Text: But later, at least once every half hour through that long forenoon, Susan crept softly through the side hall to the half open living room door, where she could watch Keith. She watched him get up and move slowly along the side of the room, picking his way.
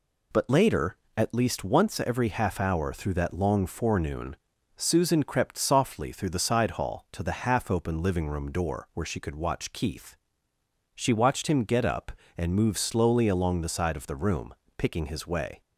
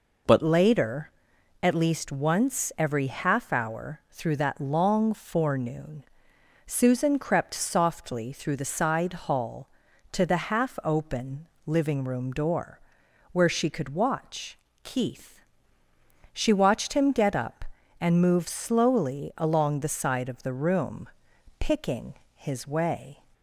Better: first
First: none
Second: changes voice at "later"; from 0.4 s on; 22.8 s long // pauses between "open" and "living"; slight; at 11.4 s; 0.20 s long // pauses between "watch" and "Keith"; slight; at 14.5 s; 0.26 s long // pauses between "picking" and "his"; slight; at 22.1 s; 0.22 s long

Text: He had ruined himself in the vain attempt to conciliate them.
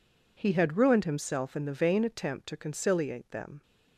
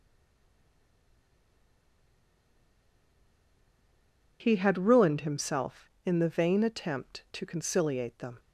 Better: first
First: none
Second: stays silent before the first word; strong; until 4.4 s; 4.4 s long

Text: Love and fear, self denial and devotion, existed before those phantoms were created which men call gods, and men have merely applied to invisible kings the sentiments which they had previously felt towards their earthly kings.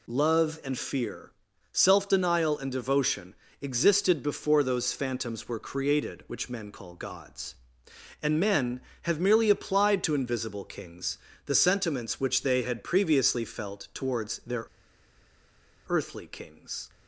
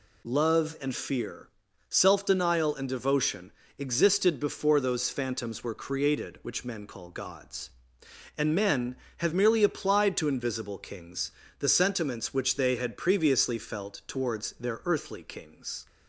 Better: second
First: pauses between "kings" and "the"; slight; at 11.1 s; 0.28 s long // pauses between "their" and "earthly"; at 14.6 s; 1.2 s long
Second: pauses between "kings" and "the"; slight; at 11.3 s; 0.28 s long

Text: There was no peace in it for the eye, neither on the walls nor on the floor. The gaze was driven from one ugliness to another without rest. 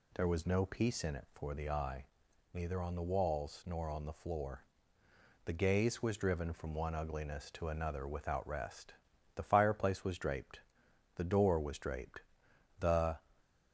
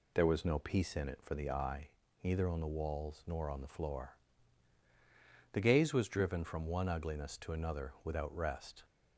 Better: second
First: goes on to say "The fireplace was draped the door was draped the"; strong; from 9.3 s on; 3.8 s long // stays silent after the last word; slight; from 13.1 s on; 0.6 s long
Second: none

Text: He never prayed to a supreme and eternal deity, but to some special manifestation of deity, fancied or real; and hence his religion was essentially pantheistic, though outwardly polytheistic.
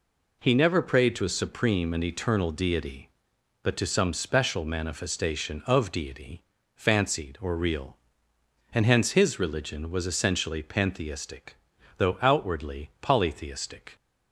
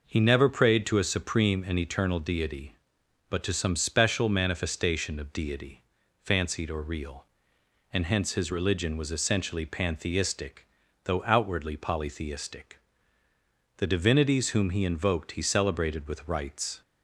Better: first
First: none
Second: goes on to say "The divinities whom he invoked he celebrated with rites"; strong; from 13.7 s on; 3.0 s long

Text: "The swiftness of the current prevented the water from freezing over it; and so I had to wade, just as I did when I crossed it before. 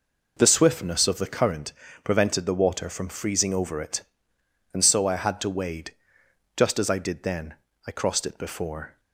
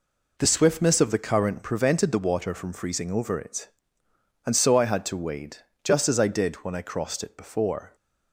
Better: second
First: pauses between "current" and "prevented"; slight; at 1.7 s; 0.32 s long // says "then" for "when"; at 7.2 s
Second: none

